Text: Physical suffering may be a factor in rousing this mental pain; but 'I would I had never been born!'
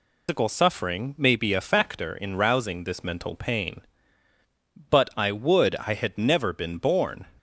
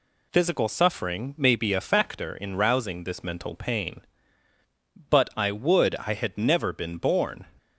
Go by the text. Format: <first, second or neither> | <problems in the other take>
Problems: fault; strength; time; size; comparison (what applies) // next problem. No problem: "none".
second | loses the start of "Physical"; at 0.2 s; 170 ms